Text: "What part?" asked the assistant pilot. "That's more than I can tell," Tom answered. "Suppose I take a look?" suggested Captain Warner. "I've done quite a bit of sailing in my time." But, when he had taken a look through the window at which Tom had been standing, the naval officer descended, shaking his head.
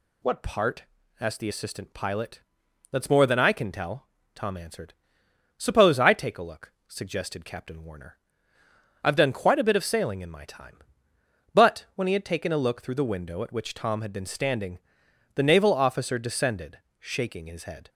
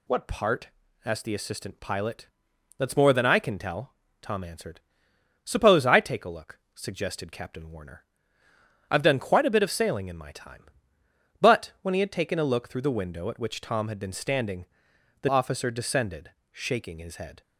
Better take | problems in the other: first | skips "naval"; at 15.2 s

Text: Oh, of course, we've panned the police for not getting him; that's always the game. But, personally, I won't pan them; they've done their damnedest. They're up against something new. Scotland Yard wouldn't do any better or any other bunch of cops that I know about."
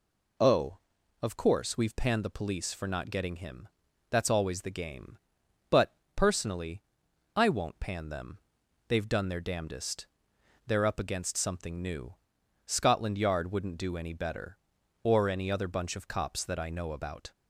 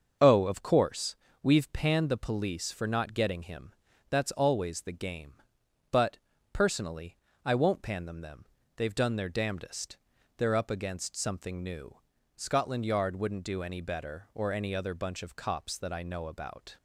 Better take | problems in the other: first | starts louder than the rest; until 1.4 s; 6.5 dB // says "them" twice; at 8.2 s

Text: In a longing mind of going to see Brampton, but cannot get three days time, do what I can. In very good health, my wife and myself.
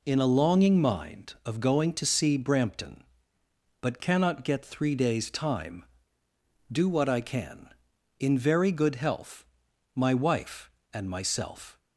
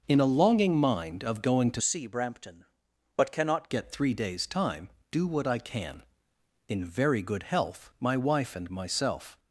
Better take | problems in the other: first | changes voice from "see" to "cannot"; from 1.8 to 3.6 s; 1.8 s long

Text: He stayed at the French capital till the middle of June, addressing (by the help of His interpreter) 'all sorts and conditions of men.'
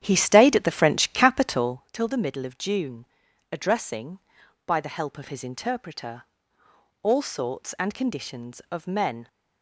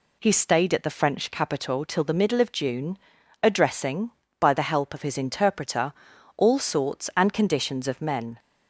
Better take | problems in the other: second | starts louder than the rest; strong; until 1.9 s; 10 dB

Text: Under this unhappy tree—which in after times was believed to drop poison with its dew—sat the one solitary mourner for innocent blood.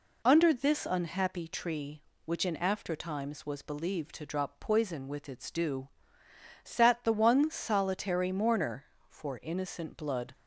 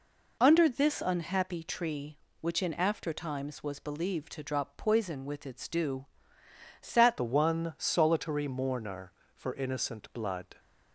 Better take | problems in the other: first | changes voice at "the"; from 7.1 s on; 3.4 s long

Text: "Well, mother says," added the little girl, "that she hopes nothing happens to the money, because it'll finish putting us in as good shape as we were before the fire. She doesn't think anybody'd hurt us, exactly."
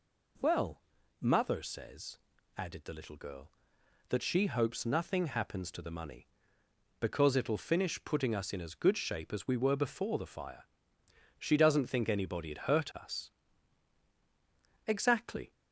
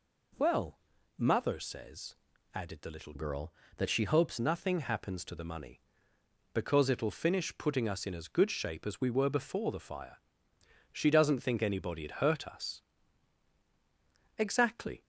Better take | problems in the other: first | changes voice from "girl" to "hopes"; from 3.1 to 4.3 s; 1.2 s long

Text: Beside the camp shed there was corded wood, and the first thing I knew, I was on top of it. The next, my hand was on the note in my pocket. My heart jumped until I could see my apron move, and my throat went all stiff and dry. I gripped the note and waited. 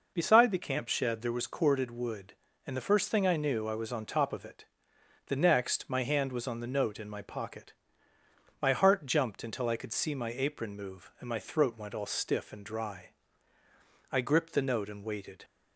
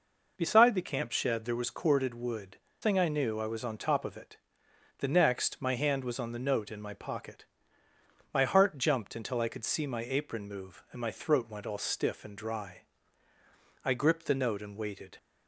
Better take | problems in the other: first | skips "and the first"; at 2.6 s

